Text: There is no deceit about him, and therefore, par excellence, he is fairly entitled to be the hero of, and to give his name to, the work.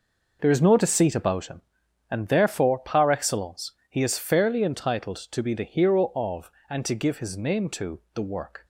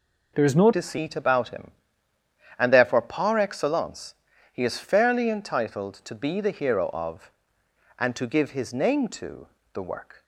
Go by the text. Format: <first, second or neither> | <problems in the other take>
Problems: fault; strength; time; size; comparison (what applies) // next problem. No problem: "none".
first | changes voice at "deceit"; from 0.7 s on; 9.5 s long